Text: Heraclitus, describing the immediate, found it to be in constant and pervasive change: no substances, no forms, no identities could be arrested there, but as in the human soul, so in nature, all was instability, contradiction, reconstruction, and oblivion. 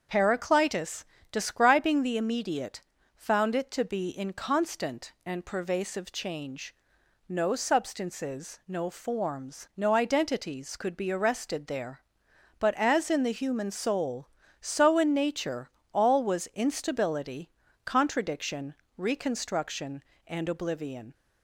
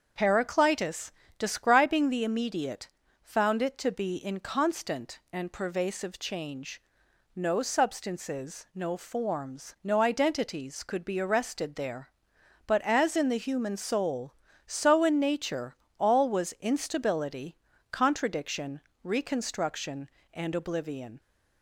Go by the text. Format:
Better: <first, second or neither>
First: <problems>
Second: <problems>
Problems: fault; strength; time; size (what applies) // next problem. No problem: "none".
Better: neither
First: starts louder than the rest; until 1.3 s; 7 dB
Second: starts louder than the rest; until 1.4 s; 7 dB